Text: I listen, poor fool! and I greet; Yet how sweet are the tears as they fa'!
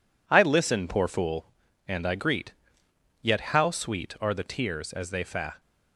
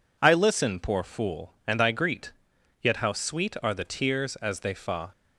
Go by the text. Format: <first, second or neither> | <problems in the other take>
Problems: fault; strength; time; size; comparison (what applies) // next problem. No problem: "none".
second | gets quieter; strong; throughout; 7.5 dB